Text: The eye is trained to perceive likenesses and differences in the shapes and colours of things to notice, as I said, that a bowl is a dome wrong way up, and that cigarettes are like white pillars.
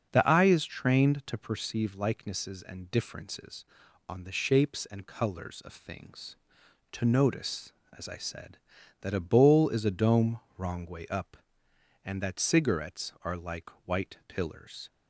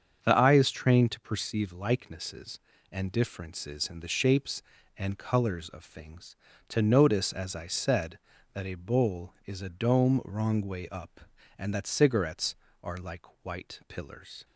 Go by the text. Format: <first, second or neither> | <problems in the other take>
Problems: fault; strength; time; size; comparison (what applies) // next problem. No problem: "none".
second | starts louder than the rest; until 1.1 s; 6.5 dB; strong in the second // says "on" for "in"; at 4.0 s // pauses between "dome" and "wrong"; slight; at 10.4 s; 0.16 s long // pauses between "like" and "white"; slight; at 13.6 s; 0.16 s long; slight in the second